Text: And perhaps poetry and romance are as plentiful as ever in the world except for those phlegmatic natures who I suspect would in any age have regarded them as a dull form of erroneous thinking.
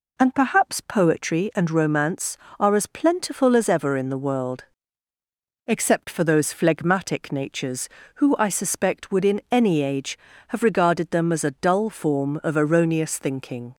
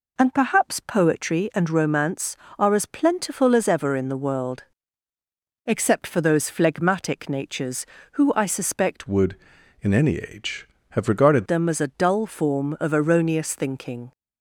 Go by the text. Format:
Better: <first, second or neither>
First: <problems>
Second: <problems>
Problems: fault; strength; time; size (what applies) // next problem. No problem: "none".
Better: first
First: pauses between "world" and "except"; at 4.6 s; 1.0 s long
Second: pauses between "world" and "except"; at 4.6 s; 1.0 s long // changes voice from "would" to "regarded"; from 9.0 to 11.4 s; 2.4 s long